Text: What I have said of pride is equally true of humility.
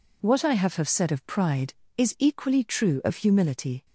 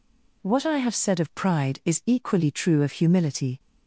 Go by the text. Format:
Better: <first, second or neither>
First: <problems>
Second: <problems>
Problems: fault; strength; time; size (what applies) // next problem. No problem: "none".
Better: second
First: says "have" twice; at 0.7 s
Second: none